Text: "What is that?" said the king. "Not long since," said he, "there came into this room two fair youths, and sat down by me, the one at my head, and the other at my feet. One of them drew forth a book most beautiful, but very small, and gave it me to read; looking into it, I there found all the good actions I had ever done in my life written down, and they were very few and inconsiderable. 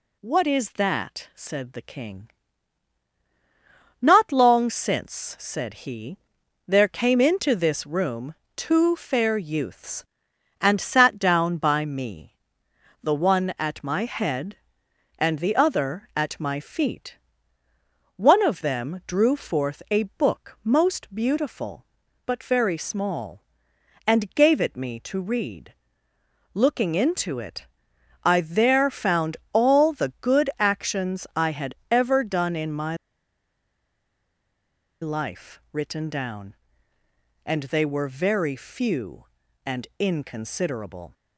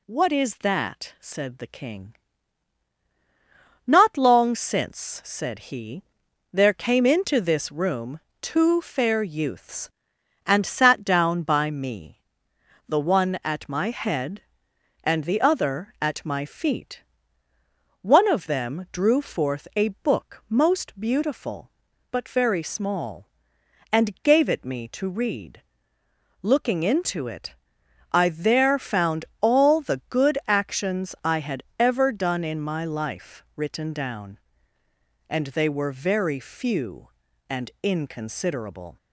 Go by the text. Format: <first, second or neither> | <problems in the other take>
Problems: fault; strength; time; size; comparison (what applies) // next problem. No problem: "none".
second | pauses between "room" and "two"; slight; at 8.3 s; 0.22 s long; slight in the second // pauses between "a" and "book"; slight; at 20.0 s; 0.16 s long; slight in the second // pauses between "found" and "all"; slight; at 29.3 s; 0.16 s long; slight in the second // pauses between "my" and "life"; strong; at 32.9 s; 2.0 s long